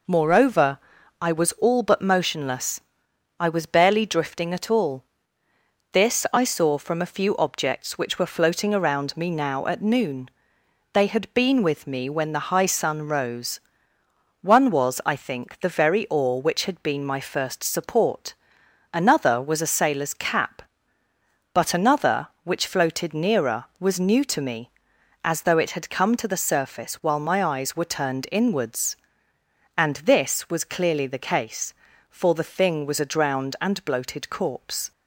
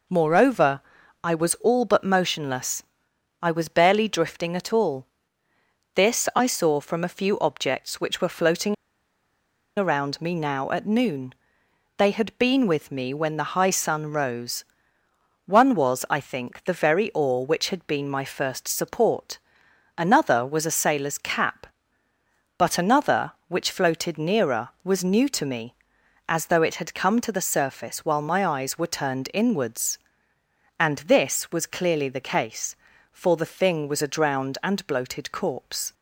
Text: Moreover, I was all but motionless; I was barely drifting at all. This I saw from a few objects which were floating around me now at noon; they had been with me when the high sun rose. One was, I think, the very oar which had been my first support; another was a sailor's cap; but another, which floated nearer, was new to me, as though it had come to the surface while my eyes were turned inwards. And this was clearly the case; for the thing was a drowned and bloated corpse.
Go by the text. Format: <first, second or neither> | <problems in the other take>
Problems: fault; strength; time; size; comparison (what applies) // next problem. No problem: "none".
first | pauses between "floating" and "around"; at 8.7 s; 1.0 s long